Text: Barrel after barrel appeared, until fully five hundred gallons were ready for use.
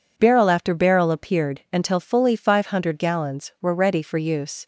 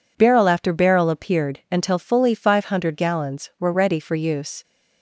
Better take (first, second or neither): neither